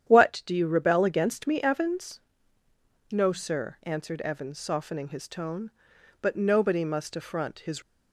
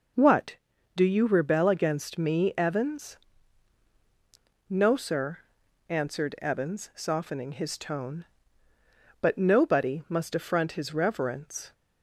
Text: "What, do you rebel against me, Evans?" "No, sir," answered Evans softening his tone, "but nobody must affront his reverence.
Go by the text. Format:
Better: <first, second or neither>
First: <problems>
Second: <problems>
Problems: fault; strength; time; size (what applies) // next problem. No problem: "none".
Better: second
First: starts louder than the rest; strong; until 1.1 s; 9.5 dB // stops before "reverence"; at 7.8 s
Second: none